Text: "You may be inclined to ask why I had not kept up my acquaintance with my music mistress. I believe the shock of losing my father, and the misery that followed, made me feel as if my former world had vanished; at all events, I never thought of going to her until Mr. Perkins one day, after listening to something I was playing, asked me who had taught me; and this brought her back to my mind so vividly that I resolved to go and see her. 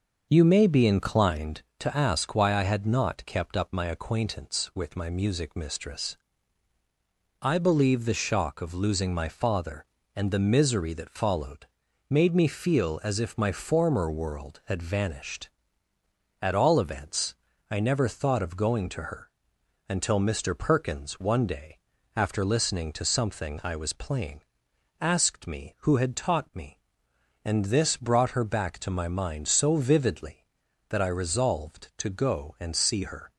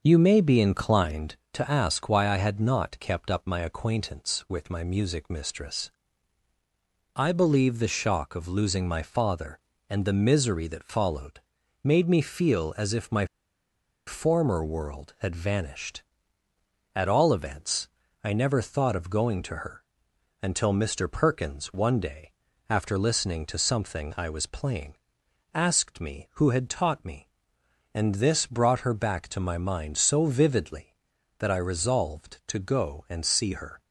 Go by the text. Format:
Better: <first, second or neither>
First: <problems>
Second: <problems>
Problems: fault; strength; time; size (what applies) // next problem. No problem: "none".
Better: first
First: starts louder than the rest; until 1.3 s; 6.5 dB // pauses between "her" and "until"; noticeable; at 19.3 s; 0.58 s long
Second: starts louder than the rest; until 1.0 s; 6.5 dB // pauses between "my" and "former"; noticeable; at 13.2 s; 0.80 s long // pauses between "her" and "until"; noticeable; at 19.8 s; 0.58 s long